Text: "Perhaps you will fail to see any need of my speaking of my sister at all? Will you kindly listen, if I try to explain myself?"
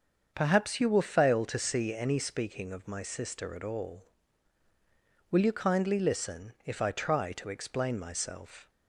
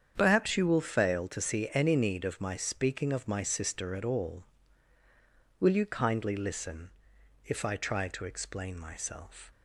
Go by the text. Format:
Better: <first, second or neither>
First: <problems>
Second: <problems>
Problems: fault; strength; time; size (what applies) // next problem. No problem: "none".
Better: second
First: starts louder than the rest; until 1.3 s; 7 dB // skips "need of my"; at 2.1 s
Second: starts louder than the rest; strong; until 1.1 s; 8 dB